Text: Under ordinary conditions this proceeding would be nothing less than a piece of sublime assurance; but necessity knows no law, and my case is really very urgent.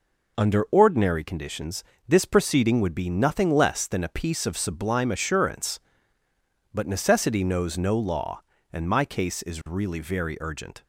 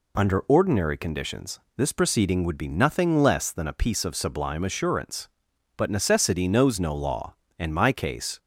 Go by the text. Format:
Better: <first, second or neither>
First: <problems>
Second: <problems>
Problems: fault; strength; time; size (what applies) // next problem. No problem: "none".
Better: first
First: pauses between "conditions" and "this"; slight; at 1.8 s; 0.24 s long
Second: pauses between "conditions" and "this"; slight; at 1.6 s; 0.16 s long // stops before "is really very urgent"; at 8.3 s